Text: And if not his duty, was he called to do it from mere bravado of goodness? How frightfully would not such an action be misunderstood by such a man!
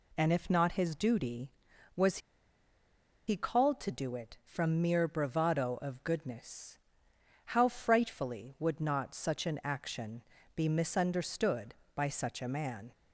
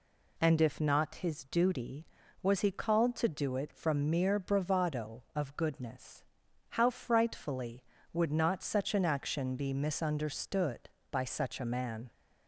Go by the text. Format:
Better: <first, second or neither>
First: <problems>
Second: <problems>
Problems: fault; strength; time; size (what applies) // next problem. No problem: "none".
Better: second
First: pauses between "was" and "he"; at 2.1 s; 1.0 s long // pauses between "action" and "be"; slight; at 10.2 s; 0.34 s long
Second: none